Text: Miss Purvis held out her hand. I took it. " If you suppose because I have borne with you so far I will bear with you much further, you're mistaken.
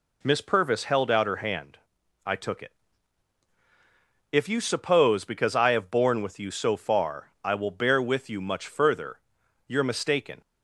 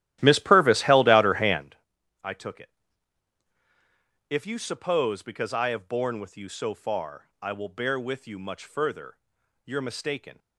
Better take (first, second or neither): first